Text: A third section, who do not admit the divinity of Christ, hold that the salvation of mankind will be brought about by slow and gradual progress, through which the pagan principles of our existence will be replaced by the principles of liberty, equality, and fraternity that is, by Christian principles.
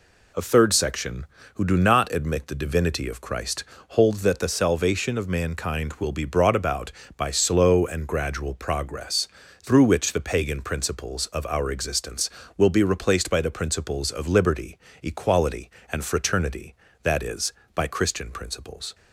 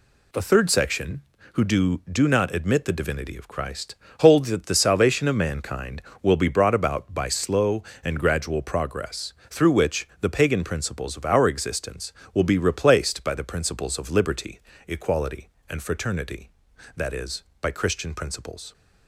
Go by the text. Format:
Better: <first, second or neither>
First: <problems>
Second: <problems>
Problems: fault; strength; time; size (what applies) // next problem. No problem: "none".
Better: first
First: none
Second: says "do" twice; at 2.0 s